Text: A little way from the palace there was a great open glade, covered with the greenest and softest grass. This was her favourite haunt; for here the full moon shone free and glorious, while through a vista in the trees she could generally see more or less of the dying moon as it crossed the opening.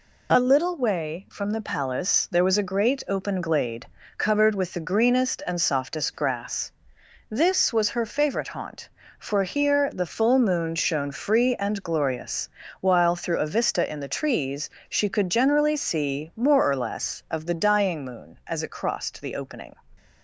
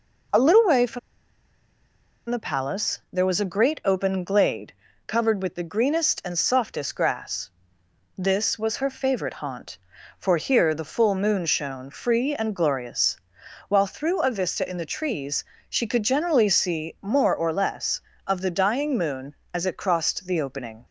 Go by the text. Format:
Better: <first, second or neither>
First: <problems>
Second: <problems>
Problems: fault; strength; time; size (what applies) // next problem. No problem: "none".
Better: first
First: pauses between "trees" and "she"; slight; at 14.6 s; 0.20 s long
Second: pauses between "from" and "the"; strong; at 0.9 s; 1.2 s long // pauses between "trees" and "she"; slight; at 15.4 s; 0.24 s long